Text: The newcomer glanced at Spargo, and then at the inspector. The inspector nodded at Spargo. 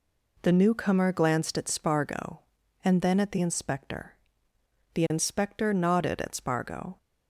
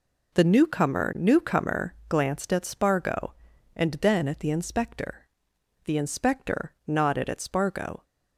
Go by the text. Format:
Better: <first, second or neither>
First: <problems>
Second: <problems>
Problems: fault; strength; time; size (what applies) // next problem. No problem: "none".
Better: first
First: none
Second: says "newcomer" twice; at 1.1 s